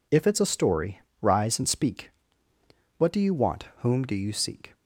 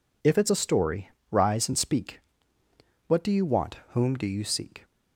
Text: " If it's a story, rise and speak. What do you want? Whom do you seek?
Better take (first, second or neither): neither